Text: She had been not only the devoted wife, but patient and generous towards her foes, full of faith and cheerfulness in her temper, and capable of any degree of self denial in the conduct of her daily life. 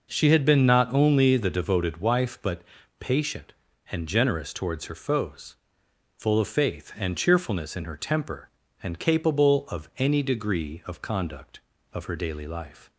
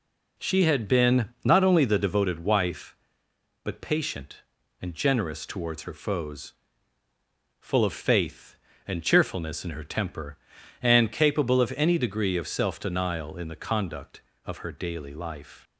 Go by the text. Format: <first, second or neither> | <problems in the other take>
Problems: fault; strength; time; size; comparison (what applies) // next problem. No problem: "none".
second | pauses between "but" and "patient"; slight; at 2.6 s; 0.36 s long // skips "self denial in the"; at 11.0 s